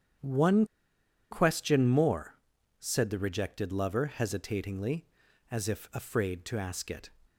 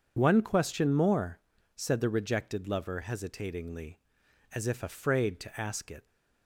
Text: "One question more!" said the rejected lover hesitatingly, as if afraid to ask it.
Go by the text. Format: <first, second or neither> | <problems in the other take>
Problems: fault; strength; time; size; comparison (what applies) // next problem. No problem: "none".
second | starts louder than the rest; strong; until 1.8 s; 8.5 dB // pauses between "One" and "question"; noticeable; at 0.6 s; 0.66 s long